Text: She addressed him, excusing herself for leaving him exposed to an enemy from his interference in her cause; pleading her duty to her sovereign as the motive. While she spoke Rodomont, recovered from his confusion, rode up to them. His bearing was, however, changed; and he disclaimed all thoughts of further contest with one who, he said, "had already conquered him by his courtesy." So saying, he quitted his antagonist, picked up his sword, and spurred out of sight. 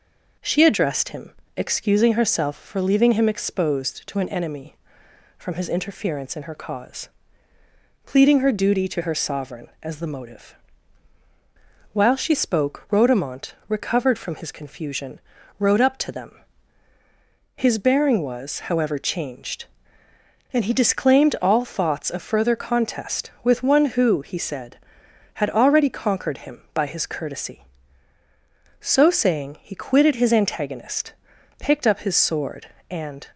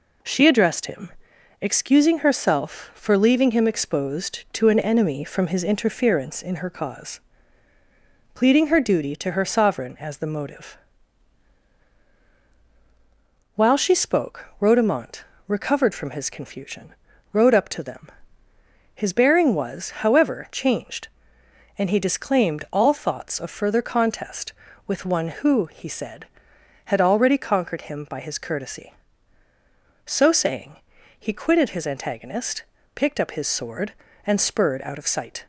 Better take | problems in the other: second | stops before "spurred out of sight"; at 33.3 s

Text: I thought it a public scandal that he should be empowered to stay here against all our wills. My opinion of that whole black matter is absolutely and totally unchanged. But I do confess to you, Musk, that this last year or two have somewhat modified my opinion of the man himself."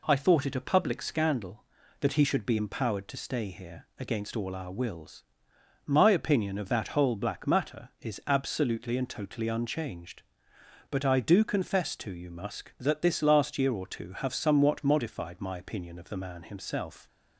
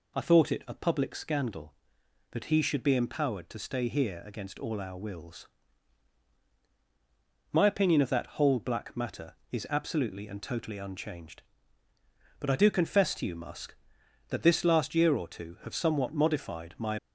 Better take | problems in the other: first | stops before "opinion of the man himself"; at 16.9 s

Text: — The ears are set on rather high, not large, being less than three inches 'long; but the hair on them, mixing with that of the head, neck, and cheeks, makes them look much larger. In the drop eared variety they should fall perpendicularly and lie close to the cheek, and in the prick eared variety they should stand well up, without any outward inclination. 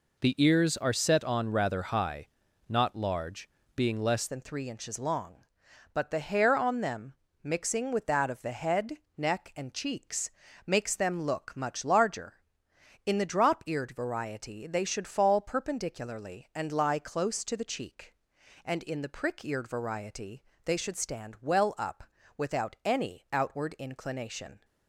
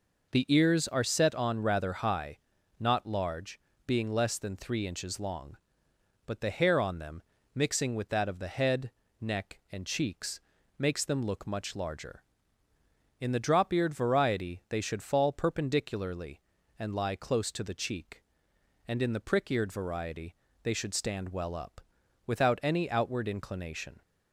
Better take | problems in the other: second | changes voice at "than"; from 4.2 s on; 20.4 s long // pauses between "variety" and "they"; slight; at 20.4 s; 0.22 s long; slight in the second

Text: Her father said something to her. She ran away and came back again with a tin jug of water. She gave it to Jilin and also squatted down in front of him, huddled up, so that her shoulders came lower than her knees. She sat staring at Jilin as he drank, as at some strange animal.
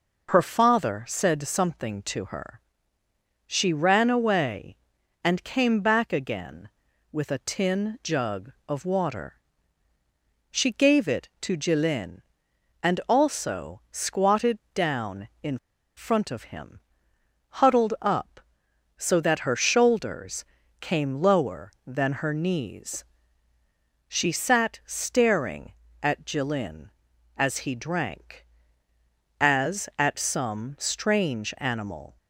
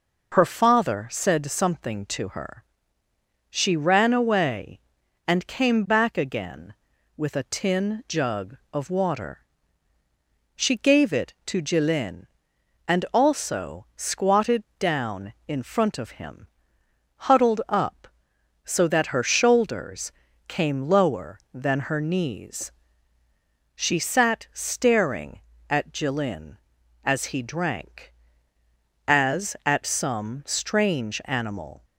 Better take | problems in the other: second | pauses between "squatted" and "down"; slight; at 14.5 s; 0.16 s long; slight in the second // pauses between "in" and "front"; at 15.5 s; 0.39 s long // pauses between "shoulders" and "came"; at 20.4 s; 0.38 s long; also in the second

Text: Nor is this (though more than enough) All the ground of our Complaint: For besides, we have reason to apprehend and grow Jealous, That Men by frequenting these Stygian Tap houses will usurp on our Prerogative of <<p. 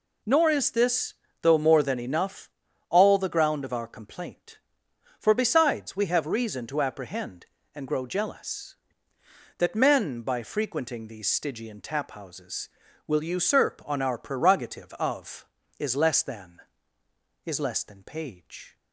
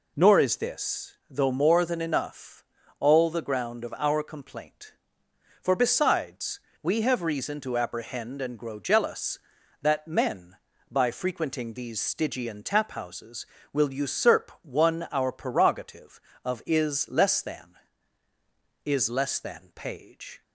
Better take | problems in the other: first | says "one" for "on"; at 14.6 s

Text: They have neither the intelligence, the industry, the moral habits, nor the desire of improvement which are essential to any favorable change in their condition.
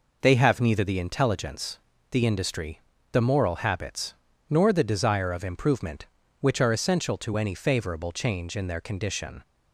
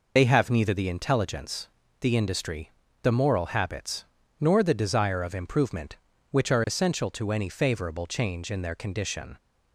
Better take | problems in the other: first | loses the start of "They"; at 0.1 s; 35 ms

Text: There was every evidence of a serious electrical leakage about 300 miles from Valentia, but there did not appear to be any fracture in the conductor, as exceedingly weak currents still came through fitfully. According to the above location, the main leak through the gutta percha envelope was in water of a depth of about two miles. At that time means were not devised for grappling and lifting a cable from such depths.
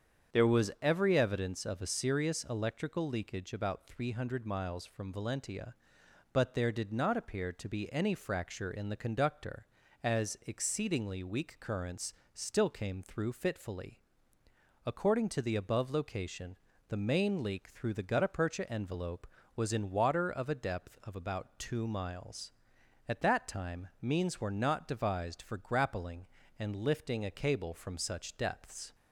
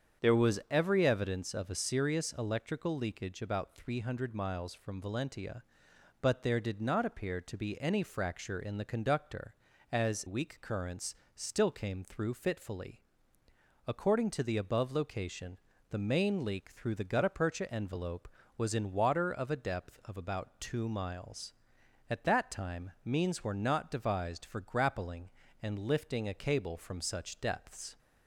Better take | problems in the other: first | starts louder than the rest; strong; until 1.3 s; 7.5 dB; strong in the first // skips "exceedingly"; at 10.2 s // pauses between "currents" and "still"; slight; at 11.1 s; 0.22 s long; slight in the first

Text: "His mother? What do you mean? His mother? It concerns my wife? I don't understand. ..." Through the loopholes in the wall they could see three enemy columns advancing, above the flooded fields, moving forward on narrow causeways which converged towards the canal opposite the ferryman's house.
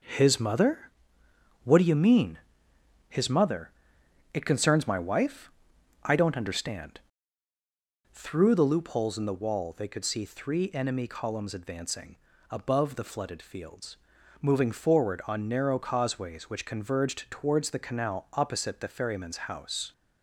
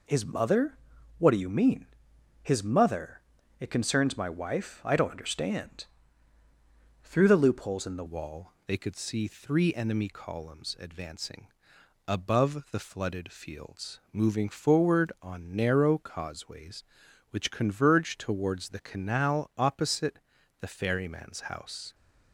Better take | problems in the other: first | changes voice at "wall"; from 8.0 s on; 13.9 s long // pauses between "opposite" and "the"; at 20.1 s; 0.40 s long

